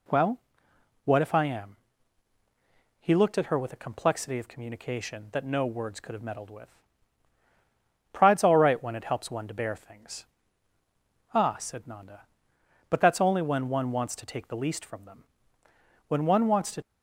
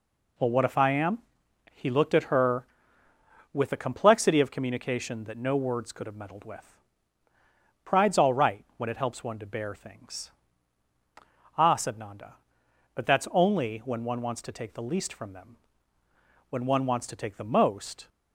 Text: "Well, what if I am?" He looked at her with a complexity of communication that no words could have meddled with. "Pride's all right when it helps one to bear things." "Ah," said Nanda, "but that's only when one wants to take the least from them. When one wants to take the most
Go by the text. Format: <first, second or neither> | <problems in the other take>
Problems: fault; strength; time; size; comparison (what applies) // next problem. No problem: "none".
second | stops before "take the most"; at 16.8 s